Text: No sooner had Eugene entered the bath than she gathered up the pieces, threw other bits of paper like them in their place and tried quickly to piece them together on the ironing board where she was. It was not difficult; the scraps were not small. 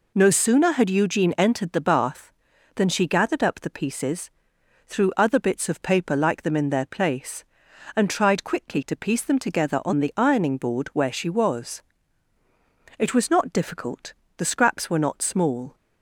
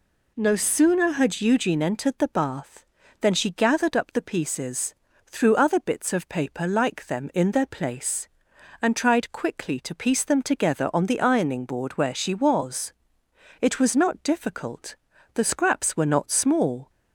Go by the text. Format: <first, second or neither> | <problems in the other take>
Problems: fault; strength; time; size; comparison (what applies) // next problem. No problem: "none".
neither | none